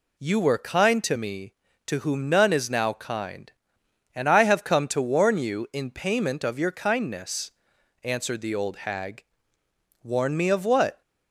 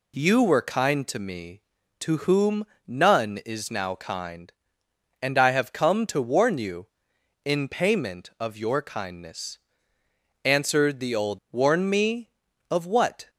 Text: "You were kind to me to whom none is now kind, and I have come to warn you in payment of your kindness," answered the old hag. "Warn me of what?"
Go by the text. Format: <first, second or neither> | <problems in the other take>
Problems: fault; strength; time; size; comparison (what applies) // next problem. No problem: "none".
first | pauses between "whom" and "none"; slight; at 2.6 s; 0.22 s long // skips "hag"; at 11.4 s